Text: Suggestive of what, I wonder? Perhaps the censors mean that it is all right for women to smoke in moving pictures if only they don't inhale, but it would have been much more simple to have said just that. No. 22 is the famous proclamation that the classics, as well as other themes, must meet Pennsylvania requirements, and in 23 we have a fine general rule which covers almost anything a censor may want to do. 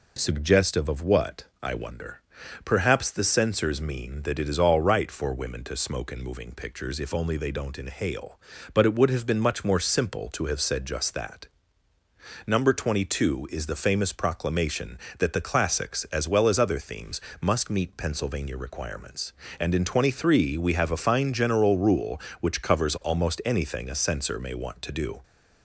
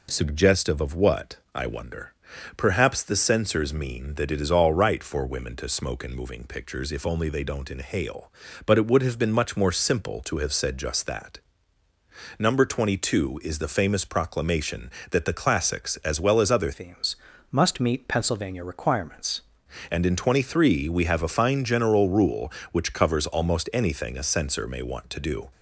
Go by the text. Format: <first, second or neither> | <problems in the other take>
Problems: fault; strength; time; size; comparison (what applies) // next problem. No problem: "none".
first | changes voice from "themes" to "requirements"; from 16.7 to 19.4 s; 2.7 s long